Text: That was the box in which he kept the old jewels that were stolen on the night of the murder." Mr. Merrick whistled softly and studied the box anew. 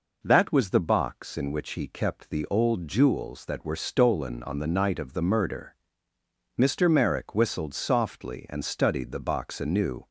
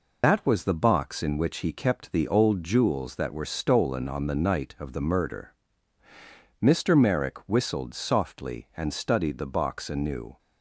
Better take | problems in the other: first | loses the start of "That"; at 0.2 s; 85 ms

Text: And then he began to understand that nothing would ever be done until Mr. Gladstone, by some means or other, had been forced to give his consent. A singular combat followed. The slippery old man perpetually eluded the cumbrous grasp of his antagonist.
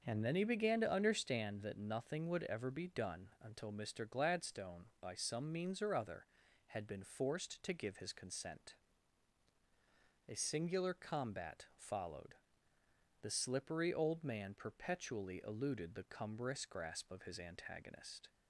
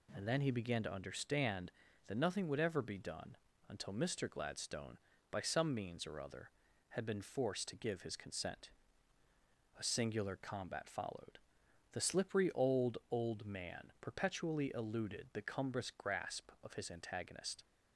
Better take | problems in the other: first | pauses between "done" and "until"; slight; at 3.3 s; 0.34 s long // says "old" twice; at 13.0 s

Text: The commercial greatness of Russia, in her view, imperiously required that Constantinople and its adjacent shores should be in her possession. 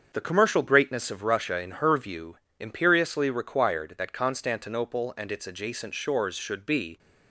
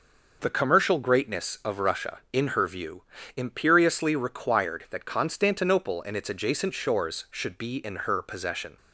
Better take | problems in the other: second | starts louder than the rest; until 1.1 s; 7 dB // stops before "in her possession"; at 6.9 s

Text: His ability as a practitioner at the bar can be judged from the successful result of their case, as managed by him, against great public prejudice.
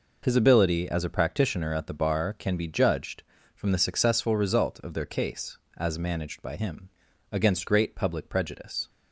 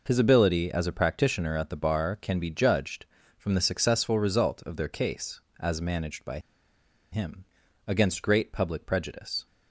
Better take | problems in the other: first | pauses between "by" and "him"; noticeable; at 6.3 s; 0.73 s long

